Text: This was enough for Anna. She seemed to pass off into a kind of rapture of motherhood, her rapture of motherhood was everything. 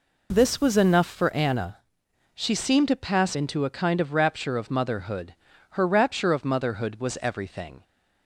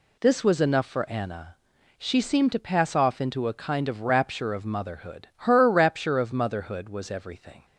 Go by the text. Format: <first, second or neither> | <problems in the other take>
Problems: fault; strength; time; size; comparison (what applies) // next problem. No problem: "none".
second | skips "off"; at 3.3 s